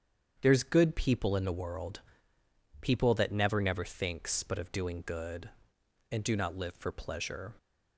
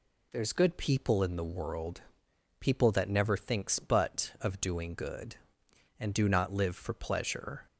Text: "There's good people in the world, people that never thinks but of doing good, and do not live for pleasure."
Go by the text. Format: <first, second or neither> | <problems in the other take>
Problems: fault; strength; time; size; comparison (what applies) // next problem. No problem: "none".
second | starts louder than the rest; strong; until 1.4 s; 8 dB // says "never" twice; at 3.6 s